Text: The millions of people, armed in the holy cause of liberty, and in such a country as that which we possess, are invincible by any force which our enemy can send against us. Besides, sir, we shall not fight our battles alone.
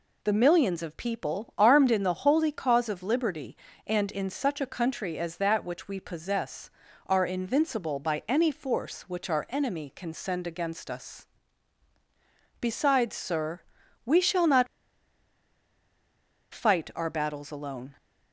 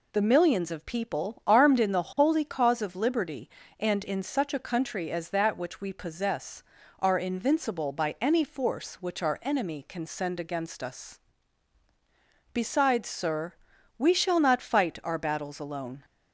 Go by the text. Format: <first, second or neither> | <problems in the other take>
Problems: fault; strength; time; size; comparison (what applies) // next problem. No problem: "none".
second | pauses between "not" and "fight"; strong; at 14.6 s; 1.8 s long